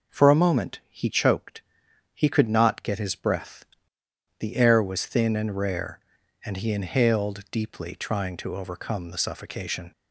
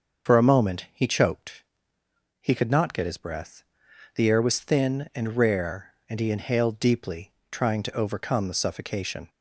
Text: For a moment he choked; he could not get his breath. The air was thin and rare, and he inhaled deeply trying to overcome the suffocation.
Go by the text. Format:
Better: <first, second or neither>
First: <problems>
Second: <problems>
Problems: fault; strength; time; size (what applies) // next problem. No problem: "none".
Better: first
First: none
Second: loses the start of "For"; at 0.2 s; 50 ms // starts louder than the rest; until 1.3 s; 6.5 dB // pauses between "deeply" and "trying"; slight; at 7.3 s; 0.20 s long